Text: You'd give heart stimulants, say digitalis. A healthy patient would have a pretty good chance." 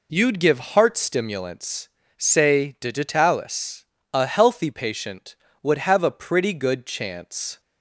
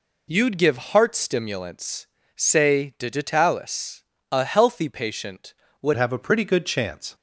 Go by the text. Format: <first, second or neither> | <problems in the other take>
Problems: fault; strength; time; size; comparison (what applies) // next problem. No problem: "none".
first | changes voice at "have"; from 5.9 s on; 1.2 s long